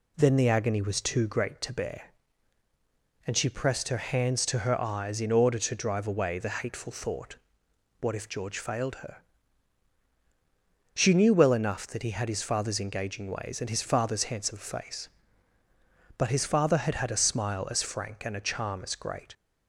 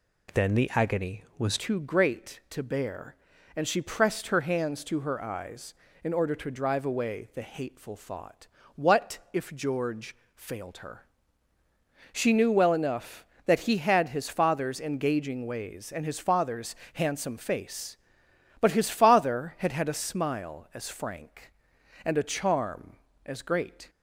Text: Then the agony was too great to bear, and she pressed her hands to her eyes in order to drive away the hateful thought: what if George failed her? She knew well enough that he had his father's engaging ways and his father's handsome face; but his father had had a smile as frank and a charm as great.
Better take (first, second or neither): first